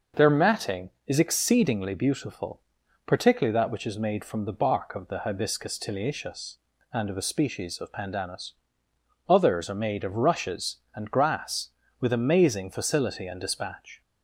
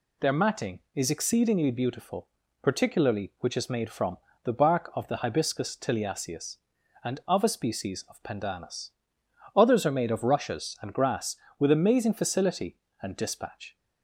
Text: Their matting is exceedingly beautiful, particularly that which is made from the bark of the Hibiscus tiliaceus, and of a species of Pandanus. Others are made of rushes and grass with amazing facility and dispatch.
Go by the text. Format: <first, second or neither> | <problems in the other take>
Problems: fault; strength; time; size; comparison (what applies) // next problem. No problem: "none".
first | skips "that"; at 3.3 s // pauses between "from" and "the"; slight; at 4.1 s; 0.28 s long